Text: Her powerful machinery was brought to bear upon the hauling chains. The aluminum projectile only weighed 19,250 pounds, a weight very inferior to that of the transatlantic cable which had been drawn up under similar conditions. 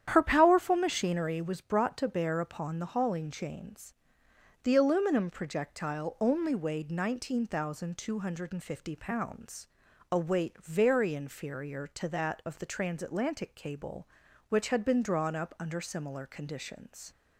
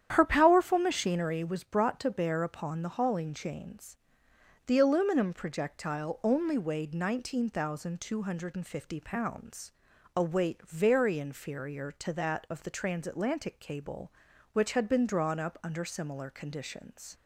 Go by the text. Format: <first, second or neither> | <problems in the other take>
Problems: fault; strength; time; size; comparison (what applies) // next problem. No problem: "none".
neither | starts louder than the rest; strong; the same in both